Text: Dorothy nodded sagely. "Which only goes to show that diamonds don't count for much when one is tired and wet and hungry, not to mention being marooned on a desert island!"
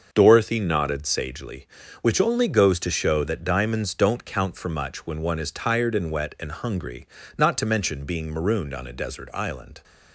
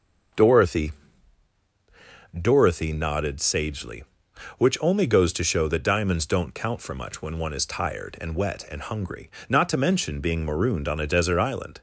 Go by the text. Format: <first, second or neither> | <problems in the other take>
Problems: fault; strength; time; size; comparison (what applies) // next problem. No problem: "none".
first | starts louder than the rest; until 2.7 s; 6.5 dB; also in the first // says "Dorothy" twice; at 2.3 s